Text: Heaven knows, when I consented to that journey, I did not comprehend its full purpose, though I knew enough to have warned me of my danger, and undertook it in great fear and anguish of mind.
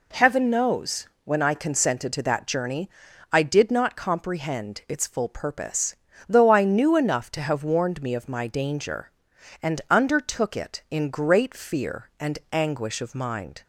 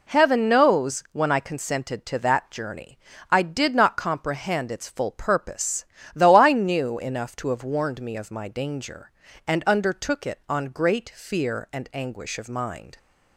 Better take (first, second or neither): first